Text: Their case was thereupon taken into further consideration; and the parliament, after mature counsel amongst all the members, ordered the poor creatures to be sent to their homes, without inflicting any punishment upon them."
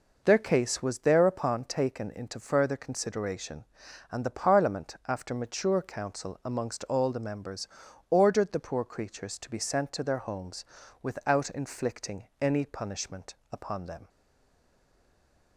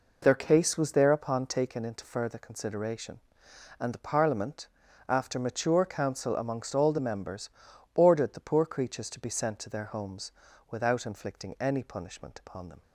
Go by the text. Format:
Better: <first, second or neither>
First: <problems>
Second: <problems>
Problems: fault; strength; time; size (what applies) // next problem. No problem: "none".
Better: second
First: pauses between "punishment" and "upon"; slight; at 13.3 s; 0.18 s long // stays silent after the last word; noticeable; from 14.0 s on; 1.5 s long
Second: none